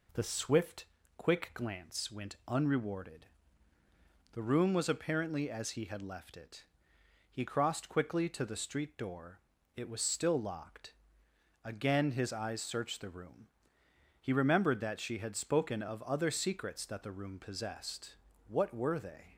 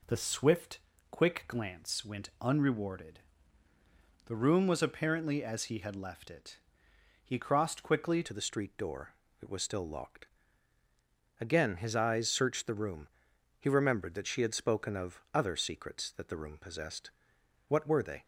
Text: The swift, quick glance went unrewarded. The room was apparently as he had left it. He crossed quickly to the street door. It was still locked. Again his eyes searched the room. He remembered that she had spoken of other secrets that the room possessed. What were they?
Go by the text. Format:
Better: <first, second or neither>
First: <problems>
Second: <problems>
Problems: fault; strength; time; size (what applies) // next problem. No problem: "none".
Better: first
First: none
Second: changes voice at "to"; from 8.2 s on; 10.0 s long